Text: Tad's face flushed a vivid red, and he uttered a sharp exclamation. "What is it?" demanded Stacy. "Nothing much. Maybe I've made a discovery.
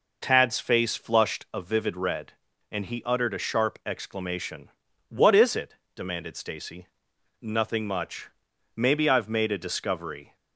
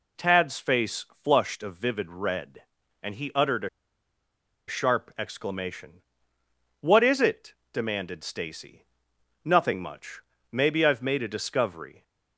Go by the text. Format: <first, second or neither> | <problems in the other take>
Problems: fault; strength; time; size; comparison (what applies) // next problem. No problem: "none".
first | pauses between "face" and "flushed"; slight; at 1.0 s; 0.18 s long // pauses between "a" and "sharp"; at 3.6 s; 0.99 s long